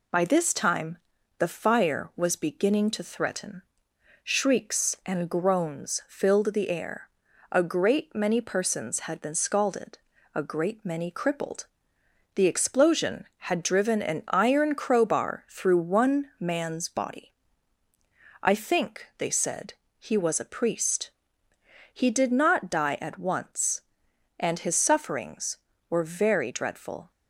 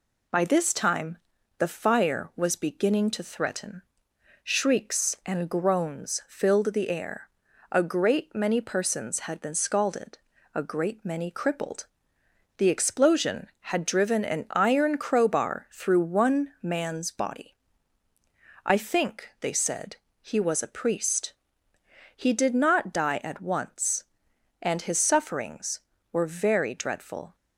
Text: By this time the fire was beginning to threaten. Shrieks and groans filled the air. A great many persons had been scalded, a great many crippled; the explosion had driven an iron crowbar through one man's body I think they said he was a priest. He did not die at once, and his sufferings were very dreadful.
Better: neither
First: pauses between "time" and "the"; at 0.9 s; 0.40 s long // pauses between "body" and "I"; at 17.3 s; 1.0 s long // pauses between "said" and "he"; slight; at 19.7 s; 0.24 s long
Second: pauses between "time" and "the"; at 1.1 s; 0.40 s long // pauses between "body" and "I"; at 17.5 s; 1.0 s long // pauses between "said" and "he"; slight; at 19.9 s; 0.24 s long

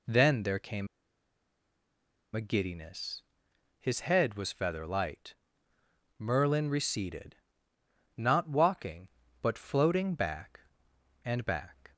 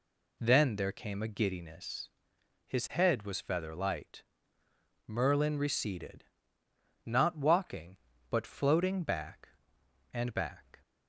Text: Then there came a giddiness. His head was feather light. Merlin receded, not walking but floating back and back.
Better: second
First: pauses between "came" and "a"; strong; at 0.8 s; 1.4 s long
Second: none

